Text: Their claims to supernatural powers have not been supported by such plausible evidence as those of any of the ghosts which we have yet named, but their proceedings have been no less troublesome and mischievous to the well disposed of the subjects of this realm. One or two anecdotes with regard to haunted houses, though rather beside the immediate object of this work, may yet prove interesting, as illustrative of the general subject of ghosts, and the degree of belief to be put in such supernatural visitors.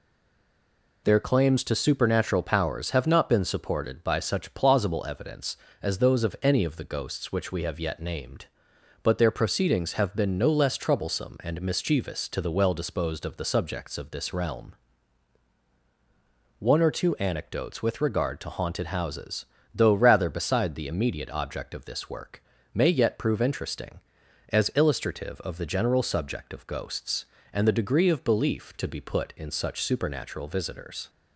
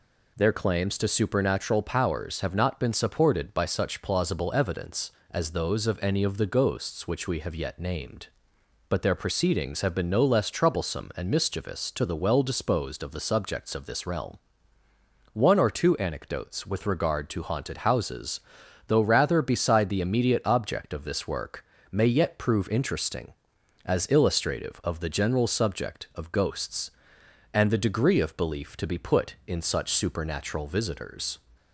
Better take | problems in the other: second | stays silent before the first word; until 1.0 s; 1.0 s long

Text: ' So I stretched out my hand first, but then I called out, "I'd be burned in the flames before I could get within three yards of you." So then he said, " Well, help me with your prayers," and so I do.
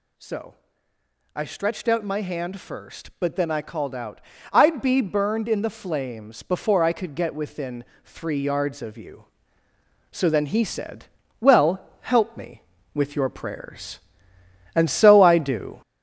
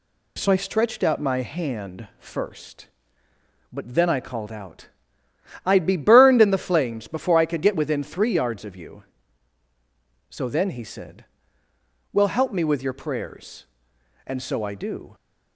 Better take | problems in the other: second | gets louder; slight; throughout; 2.5 dB // pauses between "So" and "I"; noticeable; at 0.5 s; 0.80 s long // pauses between "within" and "three"; slight; at 7.8 s; 0.22 s long

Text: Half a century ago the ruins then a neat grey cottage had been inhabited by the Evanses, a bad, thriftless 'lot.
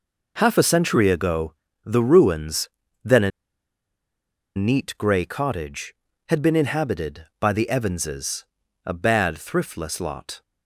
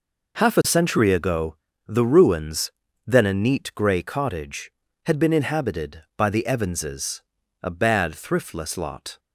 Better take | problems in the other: second | pauses between "ago" and "the"; slight; at 1.5 s; 0.28 s long; slight in the second // pauses between "ruins" and "then"; slight; at 2.6 s; 0.34 s long; slight in the second // pauses between "a" and "neat"; strong; at 3.3 s; 1.2 s long

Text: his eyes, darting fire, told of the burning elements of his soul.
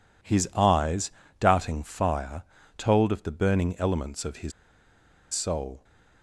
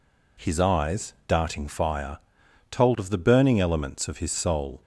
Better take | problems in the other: second | pauses between "his" and "soul"; noticeable; at 4.5 s; 0.81 s long

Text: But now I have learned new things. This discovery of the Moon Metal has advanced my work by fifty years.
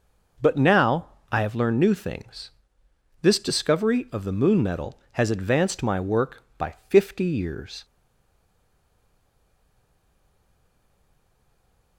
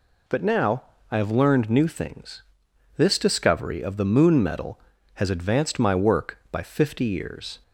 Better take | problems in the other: second | pauses between "now" and "I"; slight; at 1.0 s; 0.24 s long; slight in the second // stays silent after the last word; strong; from 7.8 s on; 4.1 s long

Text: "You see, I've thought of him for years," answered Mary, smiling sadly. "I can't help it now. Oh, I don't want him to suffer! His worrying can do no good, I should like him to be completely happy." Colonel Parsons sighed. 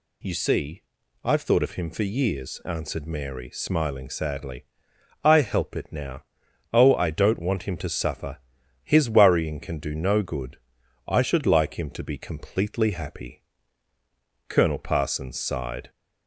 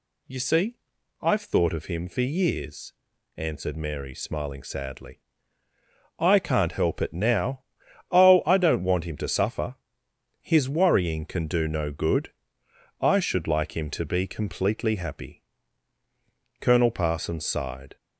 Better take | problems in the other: second | skips "can't"; at 5.3 s

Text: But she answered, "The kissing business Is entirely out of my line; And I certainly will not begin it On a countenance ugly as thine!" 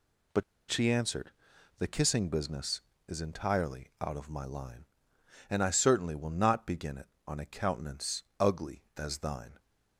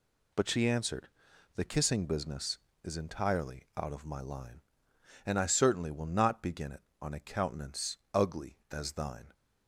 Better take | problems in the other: second | pauses between "But" and "she"; slight; at 0.4 s; 0.27 s long // pauses between "countenance" and "ugly"; slight; at 8.2 s; 0.16 s long; slight in the second

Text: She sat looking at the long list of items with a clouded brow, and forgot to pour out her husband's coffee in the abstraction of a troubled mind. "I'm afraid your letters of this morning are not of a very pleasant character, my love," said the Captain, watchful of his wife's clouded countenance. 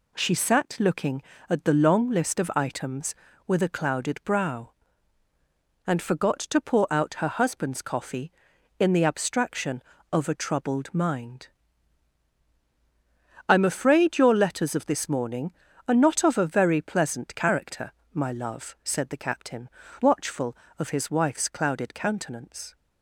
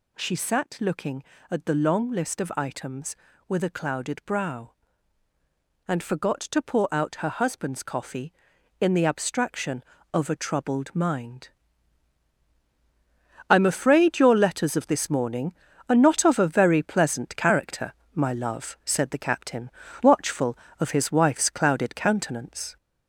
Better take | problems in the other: first | gets louder; noticeable; throughout; 4 dB

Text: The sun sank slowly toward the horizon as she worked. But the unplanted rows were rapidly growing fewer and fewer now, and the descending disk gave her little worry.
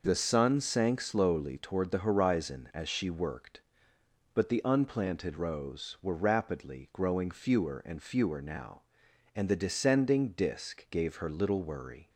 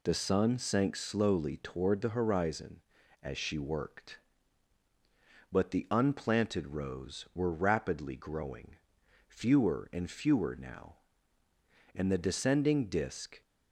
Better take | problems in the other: first | pauses between "growing" and "fewer"; noticeable; at 8.7 s; 0.52 s long // stops before "gave her little worry"; at 13.4 s

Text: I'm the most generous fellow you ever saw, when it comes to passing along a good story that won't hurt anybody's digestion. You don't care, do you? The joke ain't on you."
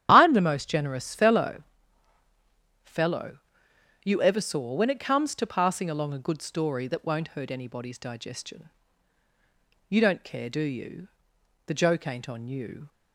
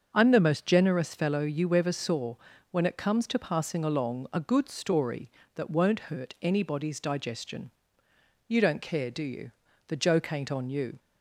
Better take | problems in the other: second | starts louder than the rest; strong; until 1.1 s; 11 dB; also in the second // says "fellow" twice; at 2.8 s

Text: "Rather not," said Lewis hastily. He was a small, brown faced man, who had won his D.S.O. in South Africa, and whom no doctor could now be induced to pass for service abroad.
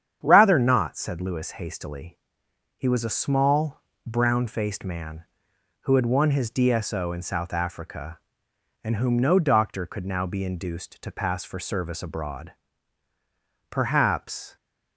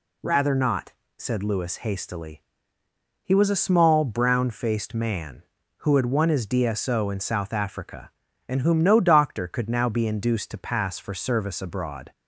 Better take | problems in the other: second | starts louder than the rest; strong; until 1.2 s; 8.5 dB // goes on to say "Perhaps"; noticeable; from 13.7 s on; 0.84 s long

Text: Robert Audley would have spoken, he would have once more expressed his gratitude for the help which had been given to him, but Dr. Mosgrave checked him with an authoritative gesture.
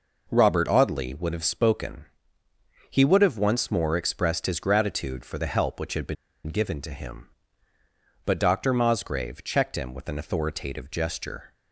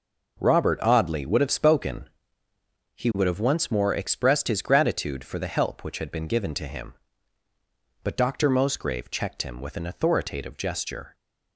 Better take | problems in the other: second | pauses between "been" and "given"; slight; at 6.1 s; 0.32 s long

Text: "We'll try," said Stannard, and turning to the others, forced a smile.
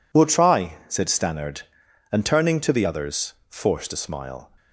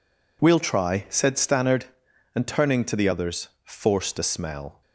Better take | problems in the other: first | says "smell" for "smile"; at 4.2 s

